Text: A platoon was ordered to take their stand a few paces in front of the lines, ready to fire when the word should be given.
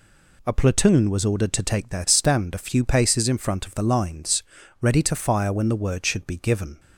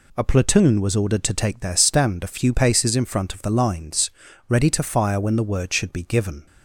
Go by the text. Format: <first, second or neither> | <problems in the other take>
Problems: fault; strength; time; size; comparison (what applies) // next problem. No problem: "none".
neither | none